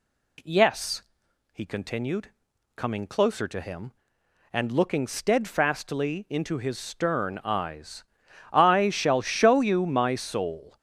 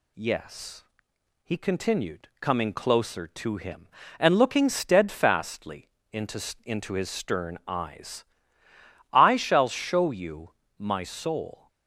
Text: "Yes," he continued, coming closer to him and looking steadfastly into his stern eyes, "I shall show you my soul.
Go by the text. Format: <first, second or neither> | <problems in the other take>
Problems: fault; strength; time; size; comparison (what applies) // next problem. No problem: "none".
first | pauses between "steadfastly" and "into"; slight; at 5.8 s; 0.24 s long // says "into" twice; at 6.6 s // pauses between "you" and "my"; slight; at 10.4 s; 0.30 s long